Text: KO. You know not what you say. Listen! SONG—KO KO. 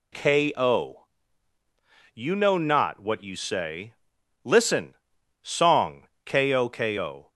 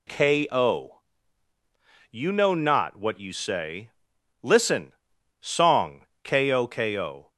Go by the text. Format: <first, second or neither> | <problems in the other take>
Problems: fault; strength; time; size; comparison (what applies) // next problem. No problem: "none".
neither | none